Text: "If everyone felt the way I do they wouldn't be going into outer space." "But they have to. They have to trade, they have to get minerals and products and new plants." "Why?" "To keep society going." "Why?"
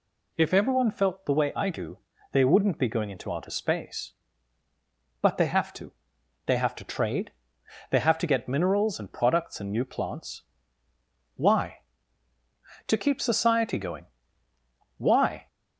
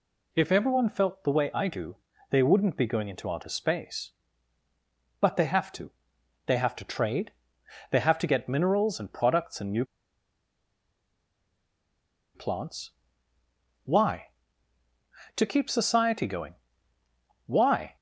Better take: first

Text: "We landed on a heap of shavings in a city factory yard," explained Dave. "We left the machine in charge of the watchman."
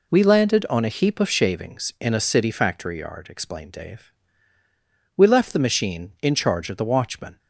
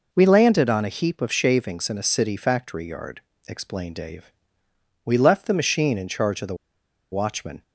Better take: first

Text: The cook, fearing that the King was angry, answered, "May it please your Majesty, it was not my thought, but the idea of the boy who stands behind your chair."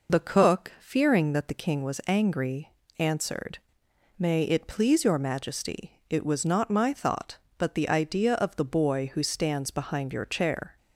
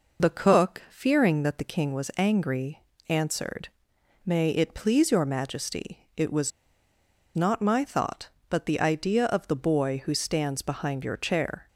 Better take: first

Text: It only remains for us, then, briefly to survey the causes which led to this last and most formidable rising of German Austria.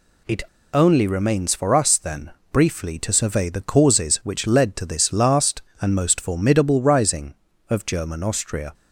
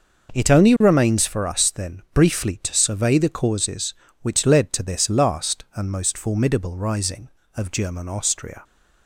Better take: second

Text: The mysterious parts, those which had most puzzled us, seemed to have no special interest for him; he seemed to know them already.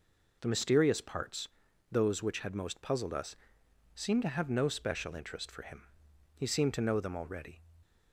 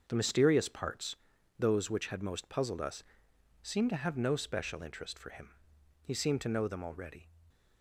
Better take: first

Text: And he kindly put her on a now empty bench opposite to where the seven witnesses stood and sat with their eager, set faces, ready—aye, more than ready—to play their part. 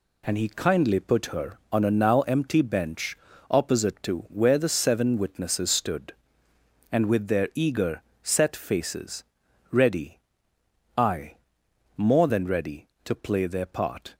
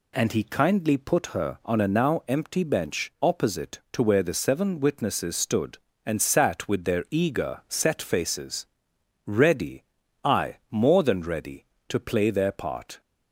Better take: second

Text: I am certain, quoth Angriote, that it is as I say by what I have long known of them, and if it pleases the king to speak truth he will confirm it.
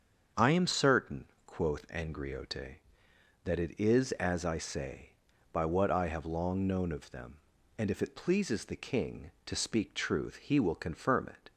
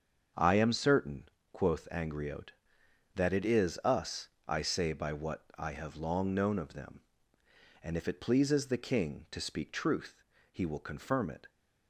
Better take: first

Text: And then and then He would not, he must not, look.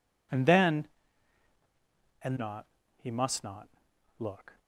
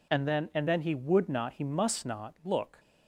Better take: second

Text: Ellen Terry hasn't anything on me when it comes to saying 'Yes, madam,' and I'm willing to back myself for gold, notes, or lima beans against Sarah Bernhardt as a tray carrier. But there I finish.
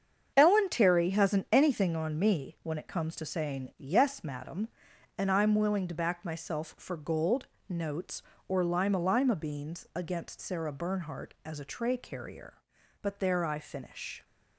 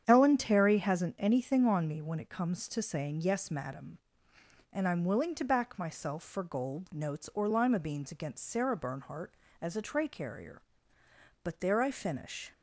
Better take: second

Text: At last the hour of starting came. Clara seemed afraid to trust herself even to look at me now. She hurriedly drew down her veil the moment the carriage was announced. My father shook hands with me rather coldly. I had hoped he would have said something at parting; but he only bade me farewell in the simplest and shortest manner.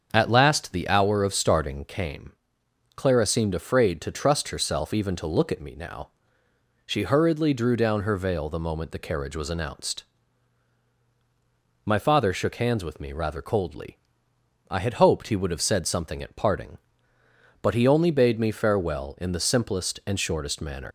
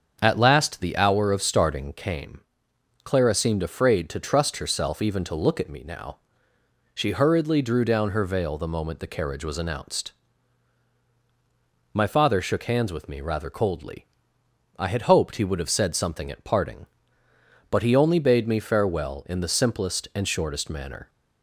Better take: second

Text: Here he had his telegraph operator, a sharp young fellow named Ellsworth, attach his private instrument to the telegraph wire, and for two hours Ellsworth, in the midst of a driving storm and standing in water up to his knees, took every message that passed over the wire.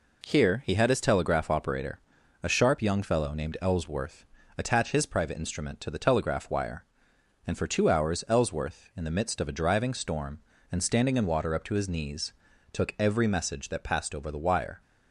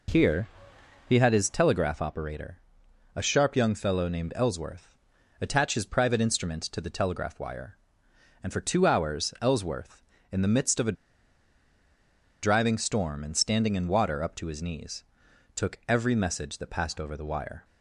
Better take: first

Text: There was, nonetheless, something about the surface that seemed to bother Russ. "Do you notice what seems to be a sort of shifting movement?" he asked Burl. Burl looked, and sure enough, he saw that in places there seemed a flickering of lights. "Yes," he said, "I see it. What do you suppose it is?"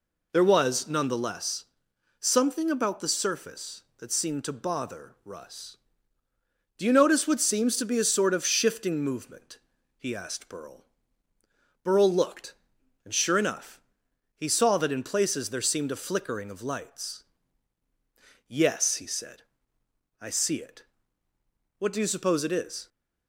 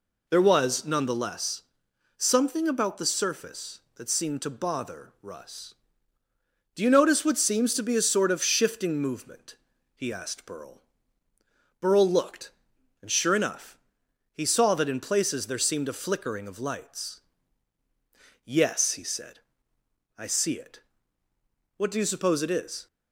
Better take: neither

